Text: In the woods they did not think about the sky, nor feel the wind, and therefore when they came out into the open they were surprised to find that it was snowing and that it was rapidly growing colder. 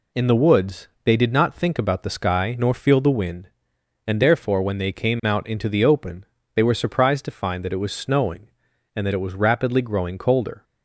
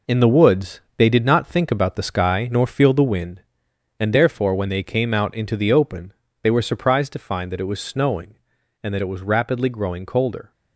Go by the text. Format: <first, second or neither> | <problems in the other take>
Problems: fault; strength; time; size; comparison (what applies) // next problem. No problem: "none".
first | gets quieter; strong; throughout; 7.5 dB // pauses between "woods" and "they"; slight; at 0.8 s; 0.16 s long; slight in the first // pauses between "open" and "they"; slight; at 6.1 s; 0.30 s long; slight in the first